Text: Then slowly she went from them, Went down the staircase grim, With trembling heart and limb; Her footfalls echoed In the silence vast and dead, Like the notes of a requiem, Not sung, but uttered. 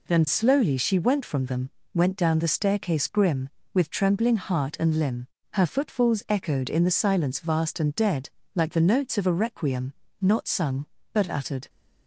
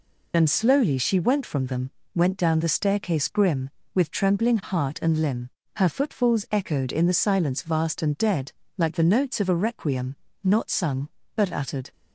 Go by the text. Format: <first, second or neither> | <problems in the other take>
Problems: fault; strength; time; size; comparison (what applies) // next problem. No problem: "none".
first | loses the start of "Then"; at 0.3 s; 45 ms